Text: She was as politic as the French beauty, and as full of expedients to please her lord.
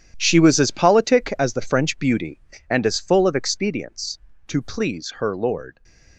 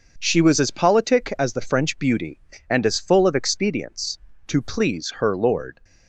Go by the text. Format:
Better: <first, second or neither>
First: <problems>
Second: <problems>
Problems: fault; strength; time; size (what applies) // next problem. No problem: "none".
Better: second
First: gets quieter; strong; throughout; 12.5 dB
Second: none